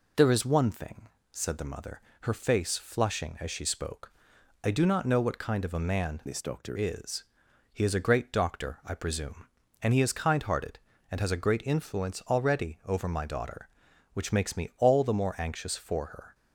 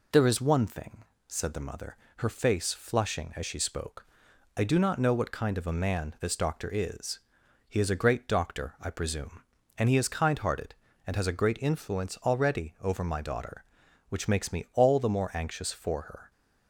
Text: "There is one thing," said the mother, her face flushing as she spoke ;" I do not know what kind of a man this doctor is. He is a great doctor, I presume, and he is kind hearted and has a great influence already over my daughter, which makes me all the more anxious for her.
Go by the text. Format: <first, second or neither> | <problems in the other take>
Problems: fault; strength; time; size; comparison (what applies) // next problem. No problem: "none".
second | changes voice from "this" to "doctor"; from 6.2 to 6.7 s; 0.5 s long